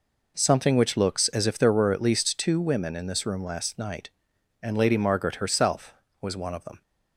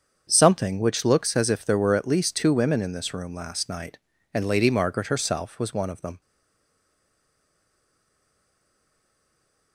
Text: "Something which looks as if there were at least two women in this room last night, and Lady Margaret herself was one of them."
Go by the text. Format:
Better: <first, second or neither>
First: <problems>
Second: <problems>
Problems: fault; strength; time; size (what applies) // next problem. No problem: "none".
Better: first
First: none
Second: starts louder than the rest; until 1.3 s; 7 dB // stays silent after the last word; strong; from 6.2 s on; 3.5 s long